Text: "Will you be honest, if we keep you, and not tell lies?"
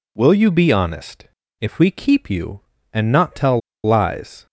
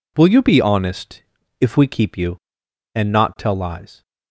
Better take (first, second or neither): second